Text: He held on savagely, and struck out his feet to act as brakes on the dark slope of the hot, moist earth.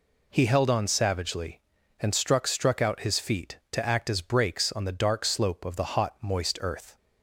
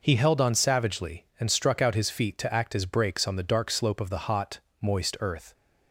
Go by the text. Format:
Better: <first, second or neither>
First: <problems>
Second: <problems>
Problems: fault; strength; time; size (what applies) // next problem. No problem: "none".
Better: second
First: says "struck" twice; at 2.4 s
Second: none